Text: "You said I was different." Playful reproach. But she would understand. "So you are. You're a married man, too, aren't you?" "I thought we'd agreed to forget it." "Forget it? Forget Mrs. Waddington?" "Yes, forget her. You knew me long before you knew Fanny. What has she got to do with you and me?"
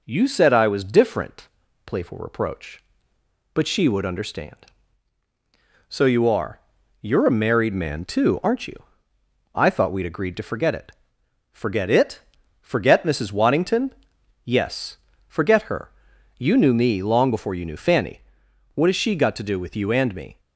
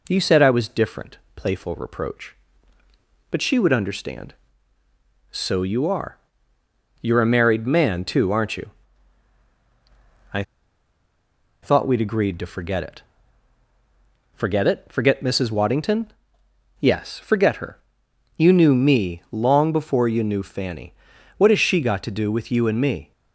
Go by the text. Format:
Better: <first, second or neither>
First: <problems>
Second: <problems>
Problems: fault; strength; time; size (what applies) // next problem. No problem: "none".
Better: first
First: none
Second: pauses between "I" and "thought"; at 10.4 s; 1.2 s long